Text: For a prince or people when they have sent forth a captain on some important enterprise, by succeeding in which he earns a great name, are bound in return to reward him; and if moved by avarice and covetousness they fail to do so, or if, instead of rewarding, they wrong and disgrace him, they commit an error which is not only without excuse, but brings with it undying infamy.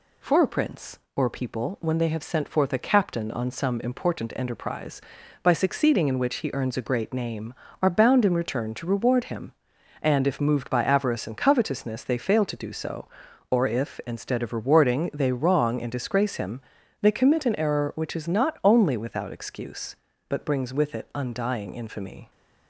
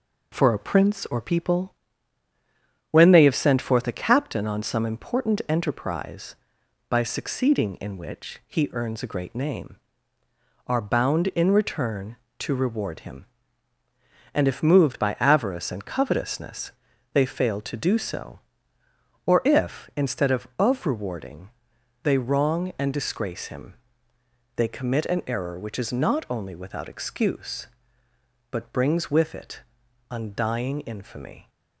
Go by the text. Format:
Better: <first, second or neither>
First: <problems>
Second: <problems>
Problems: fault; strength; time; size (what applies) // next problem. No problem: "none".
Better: first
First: none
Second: pauses between "people" and "when"; at 1.7 s; 1.1 s long // pauses between "covetousness" and "they"; at 16.7 s; 0.42 s long // says "of" twice; at 20.5 s // pauses between "it" and "undying"; noticeable; at 29.6 s; 0.50 s long